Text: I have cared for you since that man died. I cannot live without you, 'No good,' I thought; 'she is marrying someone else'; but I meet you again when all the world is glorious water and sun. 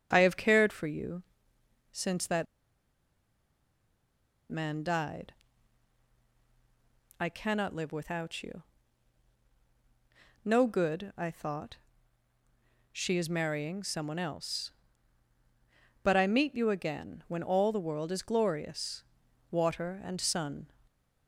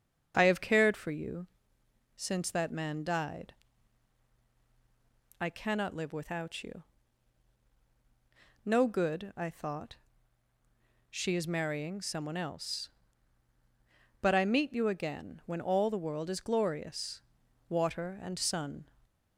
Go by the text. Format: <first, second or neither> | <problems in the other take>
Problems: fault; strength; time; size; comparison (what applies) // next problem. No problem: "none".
second | starts louder than the rest; until 1.1 s; 6.5 dB; also in the second // pauses between "you" and "since"; noticeable; at 1.2 s; 0.72 s long; noticeable in the second // pauses between "that" and "man"; strong; at 2.4 s; 2.0 s long // pauses between "glorious" and "water"; noticeable; at 19.0 s; 0.48 s long; noticeable in the second